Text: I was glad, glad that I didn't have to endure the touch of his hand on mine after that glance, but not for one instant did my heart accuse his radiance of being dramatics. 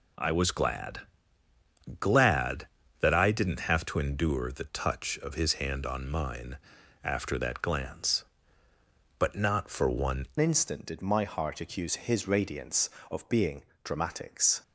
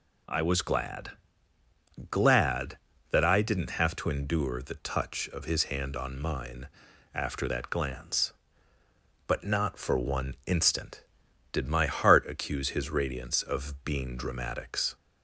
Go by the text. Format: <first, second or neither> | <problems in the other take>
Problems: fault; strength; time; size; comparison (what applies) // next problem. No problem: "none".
second | pauses between "mine" and "after"; noticeable; at 6.5 s; 0.48 s long; noticeable in the second // changes voice at "instant"; from 10.4 s on; 4.2 s long // pauses between "being" and "dramatics"; slight; at 13.6 s; 0.20 s long